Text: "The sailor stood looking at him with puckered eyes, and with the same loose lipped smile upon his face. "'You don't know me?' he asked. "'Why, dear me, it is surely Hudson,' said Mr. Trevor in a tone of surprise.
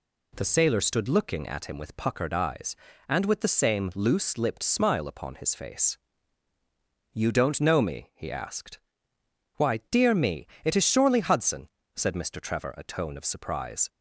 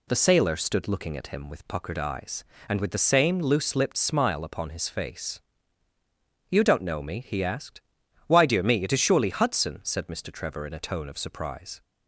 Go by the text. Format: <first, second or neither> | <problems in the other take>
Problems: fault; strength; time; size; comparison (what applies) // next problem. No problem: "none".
second | skips "in"; at 12.7 s